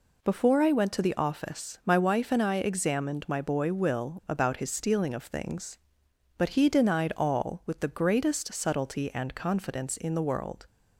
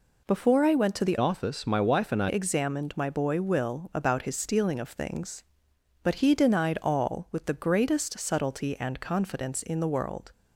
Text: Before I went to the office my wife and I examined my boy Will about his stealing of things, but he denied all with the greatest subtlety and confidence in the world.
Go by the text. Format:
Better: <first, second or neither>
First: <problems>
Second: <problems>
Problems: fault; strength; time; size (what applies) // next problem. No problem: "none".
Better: first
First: none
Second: changes voice from "office" to "I"; from 1.1 to 2.2 s; 1.1 s long